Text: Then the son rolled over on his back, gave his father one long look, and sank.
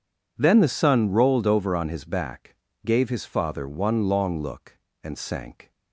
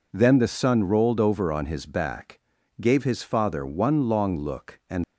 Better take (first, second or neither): first